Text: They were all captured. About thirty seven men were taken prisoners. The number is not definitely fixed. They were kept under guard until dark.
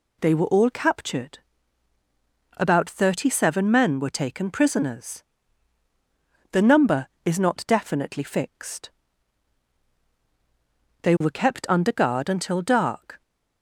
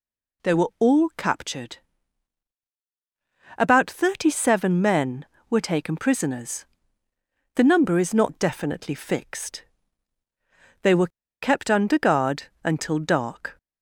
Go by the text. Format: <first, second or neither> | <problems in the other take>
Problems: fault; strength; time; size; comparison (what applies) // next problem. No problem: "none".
first | pauses between "were" and "kept"; slight; at 11.0 s; 0.34 s long // pauses between "guard" and "until"; slight; at 12.4 s; 0.20 s long